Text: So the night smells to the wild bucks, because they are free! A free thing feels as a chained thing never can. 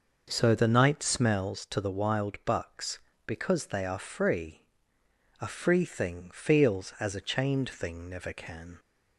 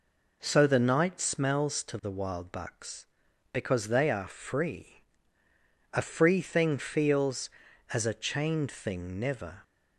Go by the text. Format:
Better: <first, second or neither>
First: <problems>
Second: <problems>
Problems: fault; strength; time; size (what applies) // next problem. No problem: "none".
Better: first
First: none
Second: stops before "can"; at 9.6 s